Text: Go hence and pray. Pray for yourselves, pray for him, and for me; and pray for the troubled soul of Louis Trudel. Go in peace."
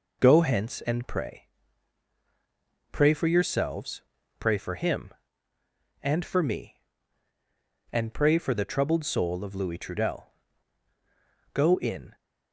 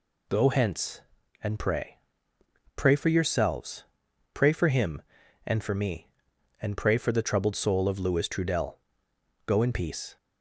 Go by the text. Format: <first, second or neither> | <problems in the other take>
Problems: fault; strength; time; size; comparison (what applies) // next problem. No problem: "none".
second | stops before "peace"; at 12.1 s